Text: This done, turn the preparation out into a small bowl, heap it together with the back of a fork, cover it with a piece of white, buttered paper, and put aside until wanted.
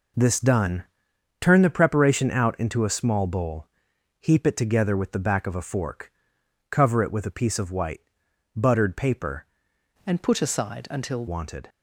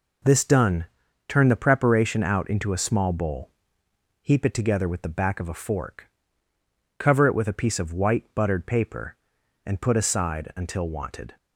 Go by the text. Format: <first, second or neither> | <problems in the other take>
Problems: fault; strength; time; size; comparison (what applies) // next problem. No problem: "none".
second | changes voice from "and" to "until"; from 10.0 to 11.2 s; 1.2 s long